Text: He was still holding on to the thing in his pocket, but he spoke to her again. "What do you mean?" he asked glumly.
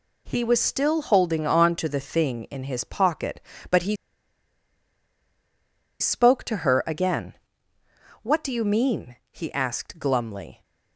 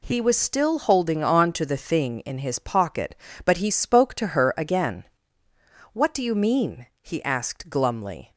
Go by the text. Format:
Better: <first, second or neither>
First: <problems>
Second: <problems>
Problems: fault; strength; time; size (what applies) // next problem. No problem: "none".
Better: second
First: pauses between "he" and "spoke"; strong; at 3.9 s; 2.0 s long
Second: none